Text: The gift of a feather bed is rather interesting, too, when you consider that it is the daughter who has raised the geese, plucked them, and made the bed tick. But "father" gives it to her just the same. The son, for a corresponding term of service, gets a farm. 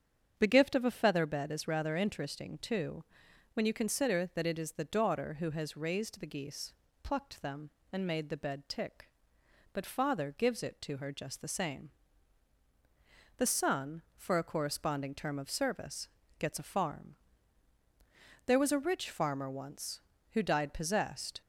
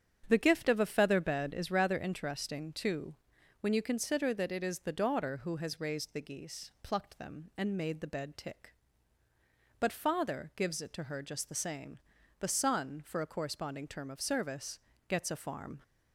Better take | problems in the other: second | starts louder than the rest; strong; until 1.3 s; 7.5 dB; strong in the second // goes on to say "There was a rich farmer once who died possessed"; strong; from 18.4 s on; 2.9 s long

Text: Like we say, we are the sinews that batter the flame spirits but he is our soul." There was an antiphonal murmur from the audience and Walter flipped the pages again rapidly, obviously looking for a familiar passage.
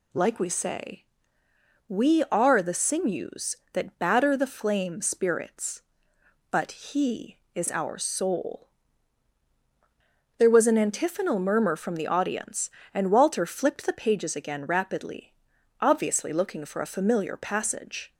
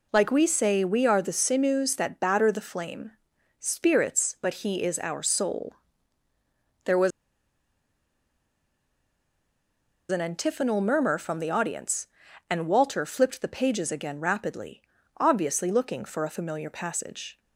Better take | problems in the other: first | pauses between "flame" and "spirits"; noticeable; at 3.1 s; 0.50 s long // pauses between "was" and "an"; strong; at 7.1 s; 2.9 s long

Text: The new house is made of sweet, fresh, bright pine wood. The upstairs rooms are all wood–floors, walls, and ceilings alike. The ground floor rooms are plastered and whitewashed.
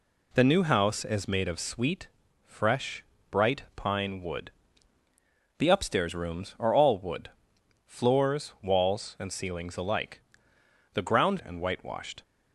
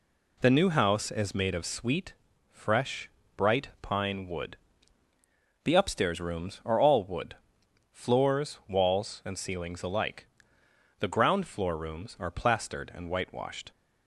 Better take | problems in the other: second | skips "floor rooms are plastered"; at 11.4 s

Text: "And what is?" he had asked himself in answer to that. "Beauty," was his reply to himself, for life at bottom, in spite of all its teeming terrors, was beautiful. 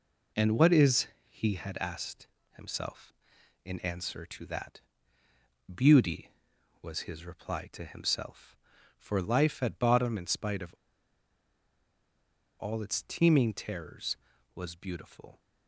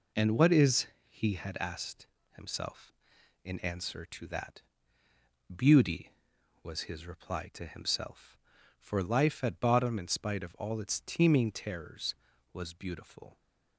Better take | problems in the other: second | pauses between "asked" and "himself"; slight; at 2.2 s; 0.24 s long; slight in the second // pauses between "of" and "all"; strong; at 10.7 s; 1.8 s long

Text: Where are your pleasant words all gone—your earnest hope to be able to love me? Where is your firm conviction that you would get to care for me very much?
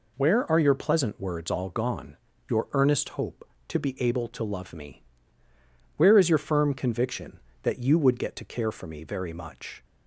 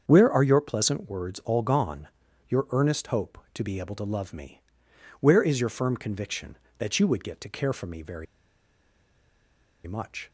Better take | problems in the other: first | starts louder than the rest; strong; until 1.0 s; 7 dB // pauses between "very" and "much"; strong; at 8.2 s; 1.6 s long

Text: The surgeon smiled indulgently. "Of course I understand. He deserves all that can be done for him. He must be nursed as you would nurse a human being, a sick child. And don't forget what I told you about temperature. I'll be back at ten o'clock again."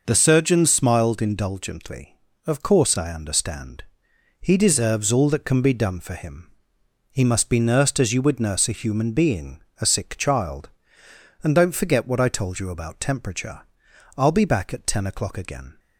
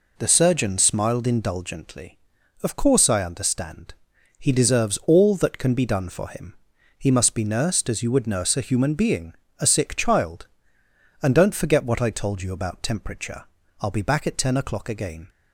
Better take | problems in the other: neither | none

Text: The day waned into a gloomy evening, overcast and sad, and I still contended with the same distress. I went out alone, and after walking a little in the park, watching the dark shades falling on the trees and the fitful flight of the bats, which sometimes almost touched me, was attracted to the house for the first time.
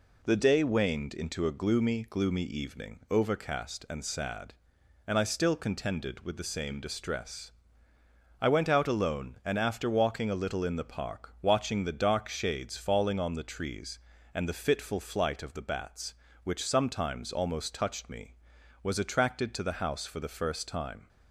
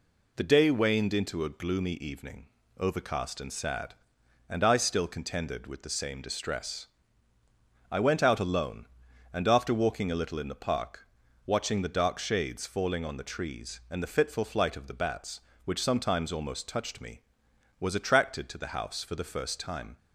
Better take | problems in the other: second | says "gloomy" twice; at 2.0 s

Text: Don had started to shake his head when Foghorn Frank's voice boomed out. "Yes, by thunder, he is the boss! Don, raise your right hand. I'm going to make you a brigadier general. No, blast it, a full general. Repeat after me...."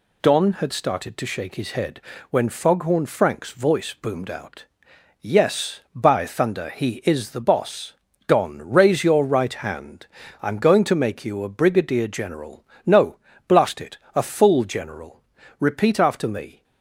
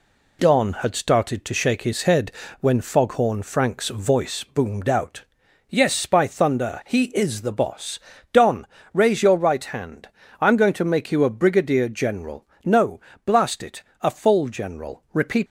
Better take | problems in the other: first | pauses between "head" and "when"; slight; at 2.3 s; 0.30 s long; slight in the first // stops before "after me"; at 15.4 s

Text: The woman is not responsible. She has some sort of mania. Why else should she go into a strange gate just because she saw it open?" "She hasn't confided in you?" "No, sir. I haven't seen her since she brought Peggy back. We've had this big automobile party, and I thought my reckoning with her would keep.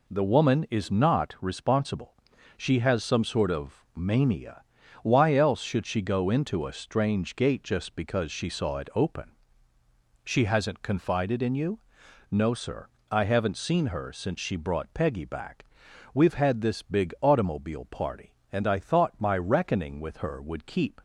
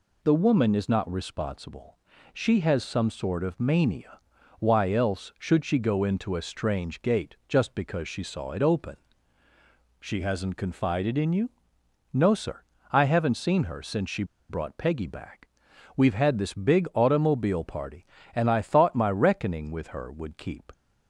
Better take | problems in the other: first | pauses between "she" and "brought"; slight; at 14.2 s; 0.25 s long

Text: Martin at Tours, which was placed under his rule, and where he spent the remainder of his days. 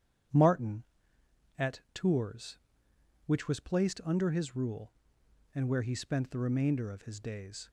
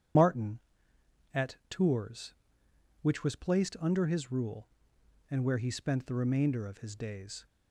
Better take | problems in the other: first | loses the start of "Martin"; at 0.1 s; 75 ms // starts louder than the rest; strong; until 2.0 s; 9 dB; strong in the first

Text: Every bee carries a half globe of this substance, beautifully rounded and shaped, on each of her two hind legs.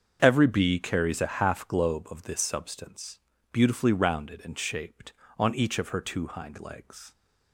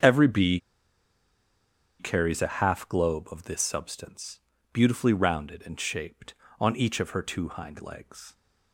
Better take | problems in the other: first | starts louder than the rest; until 2.4 s; 7 dB; also in the first // pauses between "bee" and "carries"; strong; at 0.5 s; 1.4 s long

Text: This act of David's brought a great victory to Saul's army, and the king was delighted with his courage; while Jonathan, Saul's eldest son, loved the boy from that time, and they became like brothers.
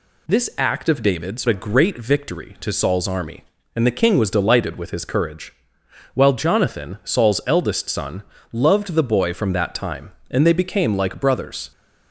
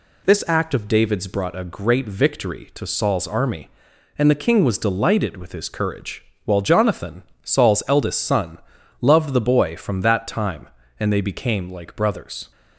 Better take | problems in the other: second | skips "brought"; at 1.4 s

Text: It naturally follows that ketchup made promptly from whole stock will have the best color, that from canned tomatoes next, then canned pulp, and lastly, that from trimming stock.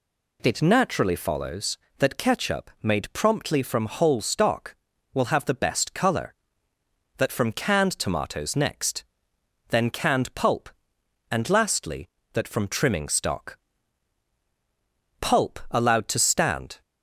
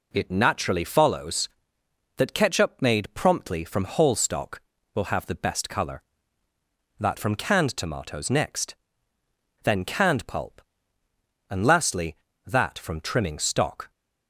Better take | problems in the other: second | goes on to say "Pulp allowed to stand"; from 15.2 s on; 1.6 s long

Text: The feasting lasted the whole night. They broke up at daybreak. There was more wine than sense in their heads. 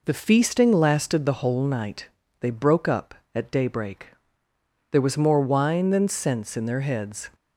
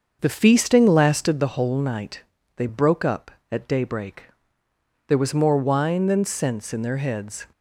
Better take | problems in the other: first | starts louder than the rest; until 1.4 s; 6.5 dB

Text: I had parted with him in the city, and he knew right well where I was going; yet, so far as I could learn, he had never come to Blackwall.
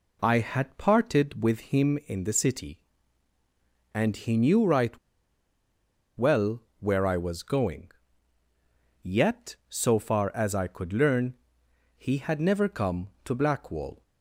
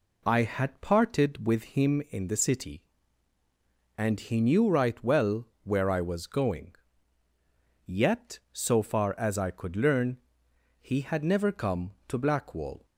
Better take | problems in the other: second | pauses between "right" and "well"; at 4.9 s; 1.2 s long // pauses between "well" and "where"; slight; at 6.6 s; 0.18 s long; slight in the second

